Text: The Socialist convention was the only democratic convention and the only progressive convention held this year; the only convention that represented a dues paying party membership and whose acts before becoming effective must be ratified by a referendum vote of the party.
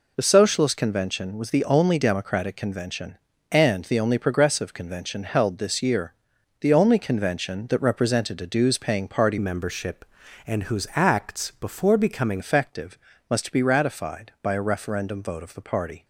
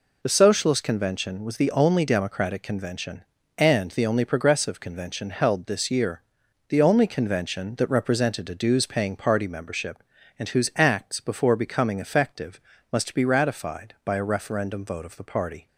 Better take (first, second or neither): second